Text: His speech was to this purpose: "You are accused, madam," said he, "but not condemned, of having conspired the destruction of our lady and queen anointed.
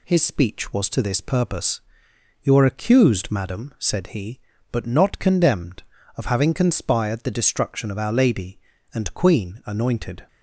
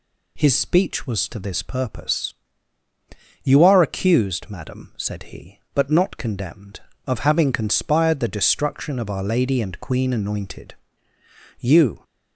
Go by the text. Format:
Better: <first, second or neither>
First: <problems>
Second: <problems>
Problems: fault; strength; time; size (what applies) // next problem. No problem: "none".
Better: first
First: none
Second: goes on to say "You"; slight; from 11.5 s on; 0.44 s long